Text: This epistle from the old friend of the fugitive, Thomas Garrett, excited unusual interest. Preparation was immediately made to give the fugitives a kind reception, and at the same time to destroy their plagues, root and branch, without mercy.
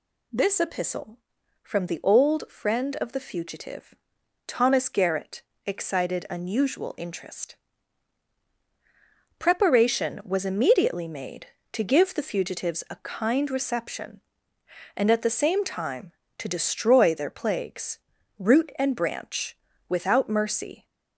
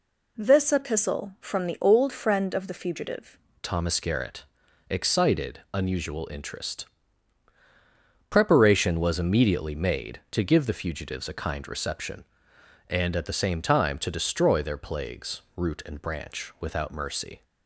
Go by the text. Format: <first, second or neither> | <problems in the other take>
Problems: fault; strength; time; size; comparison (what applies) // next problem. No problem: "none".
first | changes voice at "Thomas"; from 3.6 s on; 13.8 s long